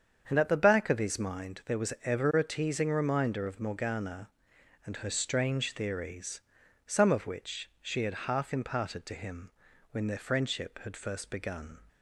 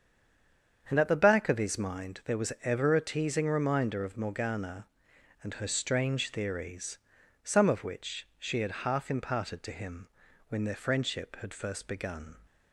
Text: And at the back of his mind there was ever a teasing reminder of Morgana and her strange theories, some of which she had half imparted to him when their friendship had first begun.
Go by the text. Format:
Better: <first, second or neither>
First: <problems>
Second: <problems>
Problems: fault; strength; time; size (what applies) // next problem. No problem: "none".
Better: first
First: starts louder than the rest; strong; until 1.3 s; 7.5 dB // pauses between "him" and "when"; at 9.4 s; 0.42 s long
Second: stays silent before the first word; slight; until 0.8 s; 0.8 s long // starts louder than the rest; strong; until 1.9 s; 7.5 dB // pauses between "him" and "when"; at 10.0 s; 0.42 s long